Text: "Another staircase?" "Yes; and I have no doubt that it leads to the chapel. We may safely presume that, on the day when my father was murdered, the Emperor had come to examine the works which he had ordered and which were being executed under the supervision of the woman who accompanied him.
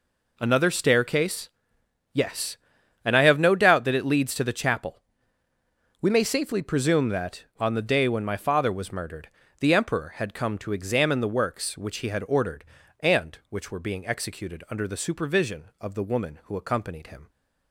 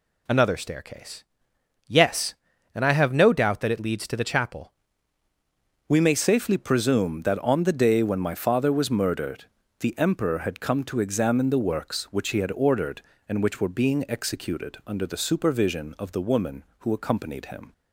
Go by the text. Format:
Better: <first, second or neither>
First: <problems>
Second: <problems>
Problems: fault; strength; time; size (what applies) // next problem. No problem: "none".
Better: first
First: none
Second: changes voice at "We"; from 5.8 s on; 11.9 s long